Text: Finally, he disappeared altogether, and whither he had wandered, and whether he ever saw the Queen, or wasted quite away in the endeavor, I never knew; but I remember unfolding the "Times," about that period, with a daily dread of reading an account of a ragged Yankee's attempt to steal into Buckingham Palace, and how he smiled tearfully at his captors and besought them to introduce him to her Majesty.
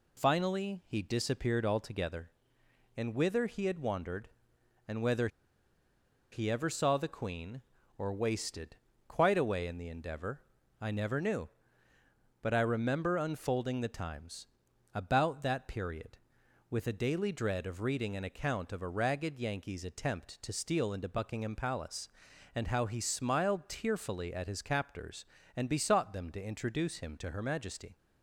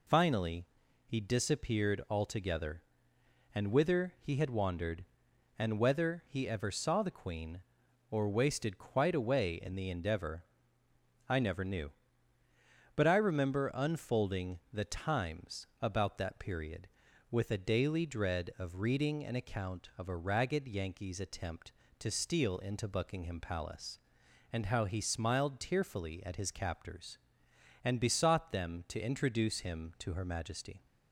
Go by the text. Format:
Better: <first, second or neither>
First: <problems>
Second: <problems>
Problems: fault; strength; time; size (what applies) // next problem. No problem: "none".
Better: second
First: pauses between "whether" and "he"; at 5.2 s; 1.0 s long // pauses between "wasted" and "quite"; slight; at 8.7 s; 0.32 s long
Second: none